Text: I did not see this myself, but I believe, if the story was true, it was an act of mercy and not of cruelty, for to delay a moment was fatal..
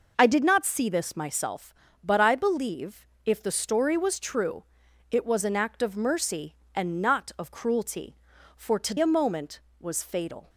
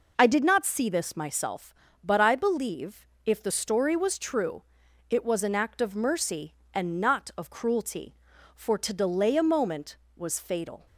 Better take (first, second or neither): second